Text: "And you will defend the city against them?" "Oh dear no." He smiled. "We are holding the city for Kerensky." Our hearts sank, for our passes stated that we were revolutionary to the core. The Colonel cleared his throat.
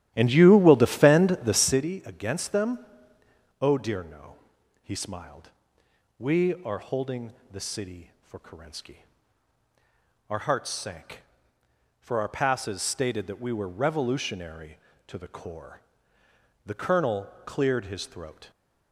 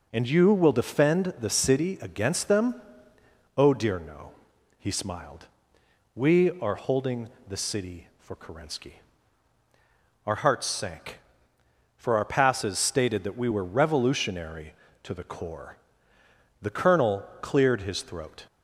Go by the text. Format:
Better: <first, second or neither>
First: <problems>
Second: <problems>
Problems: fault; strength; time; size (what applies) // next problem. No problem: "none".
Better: second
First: starts louder than the rest; strong; until 1.8 s; 12.5 dB // pauses between "holding" and "the"; slight; at 7.3 s; 0.18 s long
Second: pauses between "holding" and "the"; slight; at 7.2 s; 0.18 s long